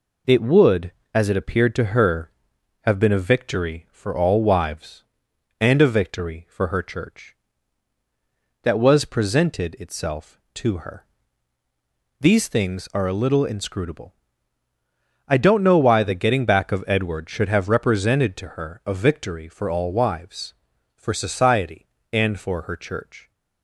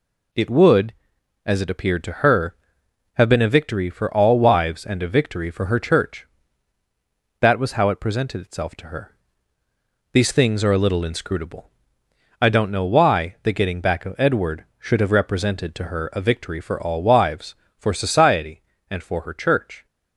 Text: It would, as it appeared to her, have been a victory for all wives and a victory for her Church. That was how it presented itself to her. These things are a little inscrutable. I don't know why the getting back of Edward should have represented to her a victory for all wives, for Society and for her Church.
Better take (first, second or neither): second